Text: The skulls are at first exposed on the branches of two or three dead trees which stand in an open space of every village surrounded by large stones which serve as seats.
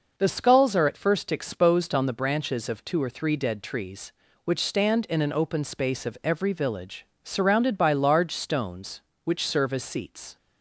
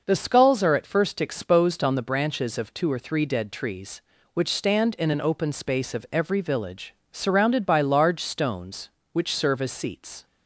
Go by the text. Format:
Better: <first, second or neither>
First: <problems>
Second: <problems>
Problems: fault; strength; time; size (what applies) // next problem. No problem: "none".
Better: neither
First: pauses between "village" and "surrounded"; slight; at 7.0 s; 0.16 s long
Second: pauses between "village" and "surrounded"; slight; at 6.9 s; 0.16 s long